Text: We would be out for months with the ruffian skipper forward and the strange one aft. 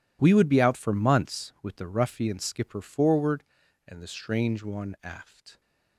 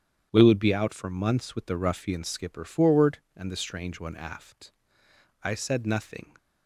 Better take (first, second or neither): first